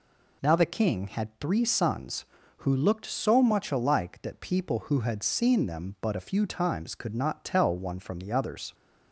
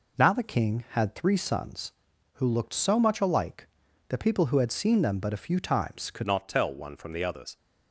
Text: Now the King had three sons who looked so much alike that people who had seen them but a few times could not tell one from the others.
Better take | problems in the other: first | changes voice at "not"; from 6.2 s on; 1.3 s long

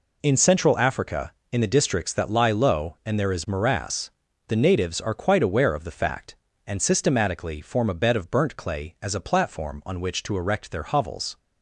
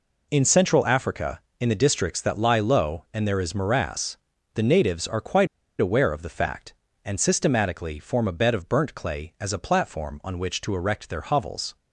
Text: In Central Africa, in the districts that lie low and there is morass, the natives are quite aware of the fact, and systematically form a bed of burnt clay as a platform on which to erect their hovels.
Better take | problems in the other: first | pauses between "quite" and "aware"; slight; at 5.4 s; 0.32 s long

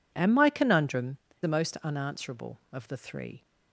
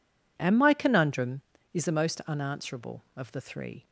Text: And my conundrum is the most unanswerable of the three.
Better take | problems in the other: second | skips "is"; at 1.3 s

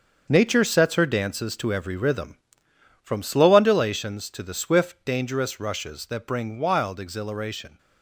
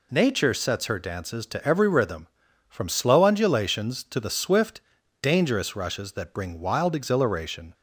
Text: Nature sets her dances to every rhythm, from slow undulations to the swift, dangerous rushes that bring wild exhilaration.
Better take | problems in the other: second | gets quieter; strong; throughout; 9.5 dB

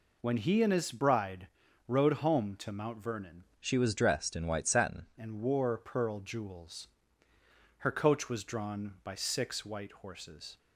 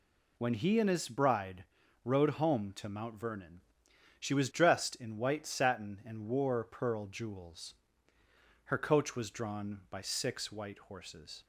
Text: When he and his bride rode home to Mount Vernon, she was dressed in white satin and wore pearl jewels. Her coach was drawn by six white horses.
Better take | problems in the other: second | pauses between "bride" and "rode"; at 1.4 s; 0.40 s long; also in the second // changes voice from "she" to "satin"; from 3.5 to 5.0 s; 1.5 s long

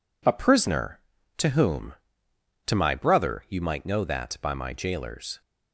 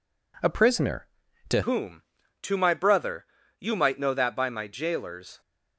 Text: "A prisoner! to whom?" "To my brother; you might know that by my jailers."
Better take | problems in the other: first | changes voice at "whom"; from 1.6 s on; 3.8 s long

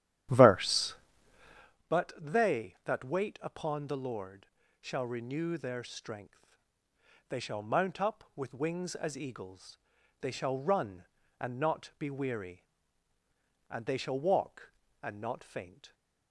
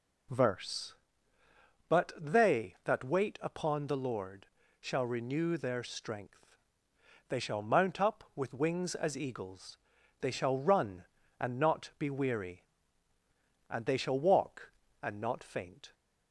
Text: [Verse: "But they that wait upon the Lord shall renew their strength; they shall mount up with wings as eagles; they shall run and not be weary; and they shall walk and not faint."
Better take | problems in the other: second | starts louder than the rest; strong; until 1.8 s; 11.5 dB // pauses between "Lord" and "shall"; slight; at 4.4 s; 0.34 s long; slight in the second

